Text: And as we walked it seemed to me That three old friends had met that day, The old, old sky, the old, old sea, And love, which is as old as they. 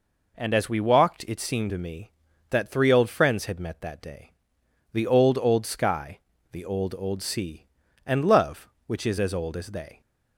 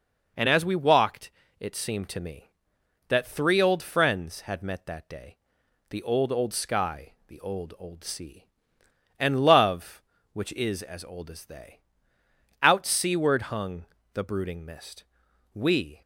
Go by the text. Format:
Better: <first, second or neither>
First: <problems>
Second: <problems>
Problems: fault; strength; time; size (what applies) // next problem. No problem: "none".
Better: first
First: none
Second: pauses between "walked" and "it"; slight; at 1.3 s; 0.28 s long // goes on to say "Out seaward hung the brooding mist We"; strong; from 12.6 s on; 3.3 s long